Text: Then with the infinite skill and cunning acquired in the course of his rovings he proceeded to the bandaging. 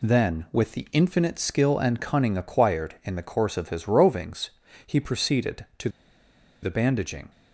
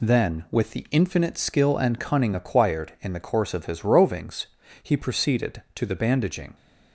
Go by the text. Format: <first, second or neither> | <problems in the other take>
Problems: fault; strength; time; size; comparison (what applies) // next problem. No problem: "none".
second | pauses between "rovings" and "he"; slight; at 4.4 s; 0.36 s long; slight in the second // pauses between "to" and "the"; noticeable; at 5.8 s; 0.74 s long